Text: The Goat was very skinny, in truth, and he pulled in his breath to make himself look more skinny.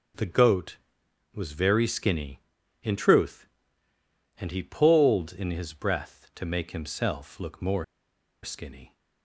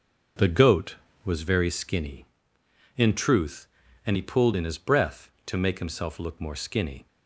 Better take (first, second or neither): second